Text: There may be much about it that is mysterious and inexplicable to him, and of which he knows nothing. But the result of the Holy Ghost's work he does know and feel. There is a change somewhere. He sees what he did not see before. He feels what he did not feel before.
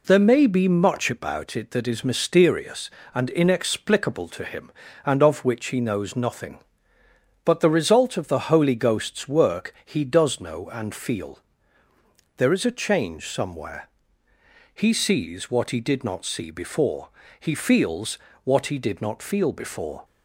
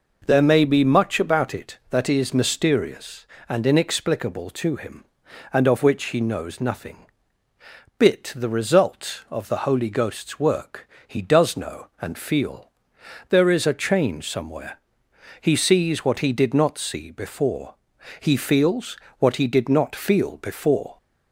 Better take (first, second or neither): first